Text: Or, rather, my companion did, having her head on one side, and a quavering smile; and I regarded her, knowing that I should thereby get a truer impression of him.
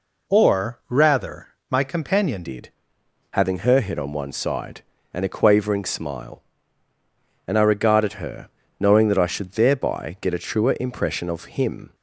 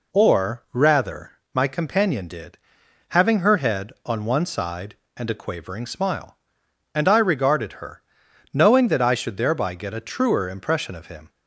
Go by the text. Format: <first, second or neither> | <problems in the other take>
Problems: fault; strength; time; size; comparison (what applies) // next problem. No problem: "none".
second | changes voice at "did"; from 2.4 s on; 9.5 s long